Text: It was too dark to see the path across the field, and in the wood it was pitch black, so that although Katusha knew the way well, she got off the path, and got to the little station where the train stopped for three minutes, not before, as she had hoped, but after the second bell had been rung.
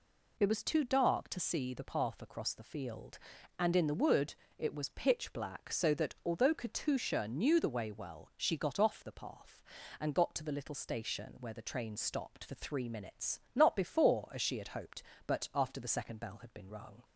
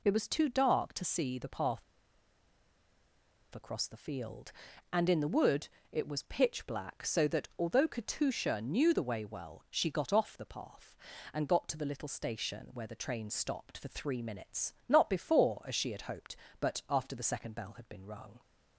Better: first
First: pauses between "wood" and "it"; slight; at 4.3 s; 0.24 s long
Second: pauses between "path" and "across"; strong; at 1.8 s; 1.7 s long // pauses between "wood" and "it"; slight; at 5.6 s; 0.24 s long

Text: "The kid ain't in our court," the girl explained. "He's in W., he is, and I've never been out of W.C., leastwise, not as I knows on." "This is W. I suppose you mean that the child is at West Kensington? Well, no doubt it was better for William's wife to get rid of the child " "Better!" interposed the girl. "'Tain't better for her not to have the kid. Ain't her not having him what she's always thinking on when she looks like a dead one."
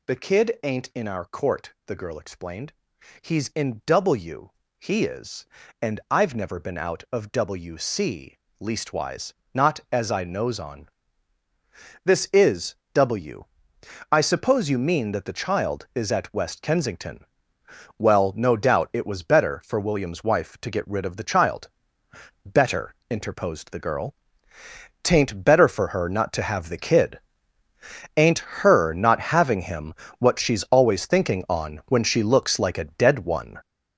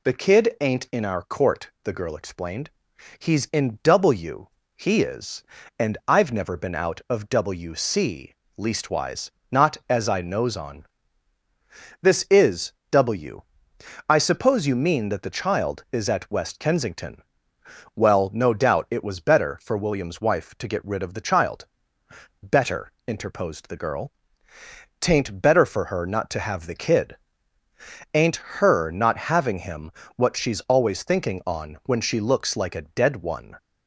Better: second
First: gets louder; throughout; 6.5 dB // pauses between "is" and "W"; slight; at 12.7 s; 0.20 s long // pauses between "him" and "what"; slight; at 29.9 s; 0.28 s long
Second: pauses between "is" and "W"; slight; at 12.7 s; 0.20 s long // pauses between "him" and "what"; slight; at 29.8 s; 0.28 s long

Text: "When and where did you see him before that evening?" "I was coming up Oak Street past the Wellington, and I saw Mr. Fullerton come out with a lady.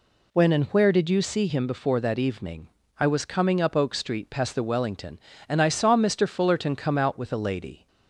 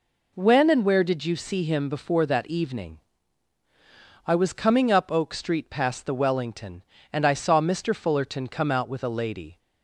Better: neither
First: none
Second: none

